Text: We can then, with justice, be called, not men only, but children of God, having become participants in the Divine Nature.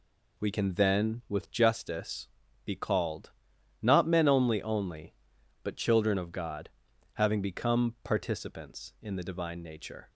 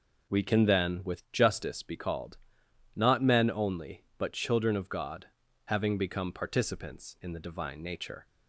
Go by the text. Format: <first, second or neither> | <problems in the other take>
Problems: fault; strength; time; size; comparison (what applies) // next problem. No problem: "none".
second | says "only" twice; at 4.6 s